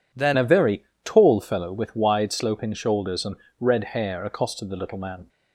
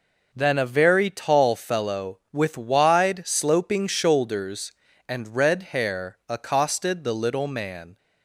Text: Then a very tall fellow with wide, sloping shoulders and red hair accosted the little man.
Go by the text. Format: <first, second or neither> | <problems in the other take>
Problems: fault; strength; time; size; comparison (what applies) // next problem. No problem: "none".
second | changes voice at "a"; from 0.3 s on; 4.9 s long // pauses between "very" and "tall"; slight; at 0.8 s; 0.22 s long // pauses between "and" and "red"; slight; at 3.3 s; 0.24 s long